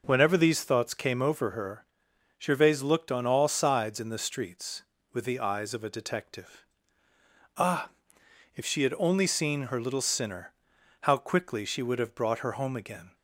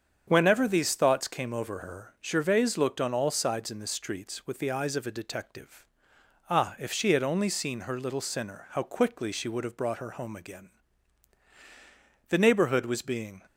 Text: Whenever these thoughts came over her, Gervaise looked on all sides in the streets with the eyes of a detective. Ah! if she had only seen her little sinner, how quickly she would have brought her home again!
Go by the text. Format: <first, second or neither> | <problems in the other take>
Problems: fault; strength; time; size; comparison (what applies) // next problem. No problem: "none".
first | starts louder than the rest; strong; until 1.2 s; 7.5 dB // goes on to say "The neighborhood was being"; noticeable; from 12.2 s on; 1.1 s long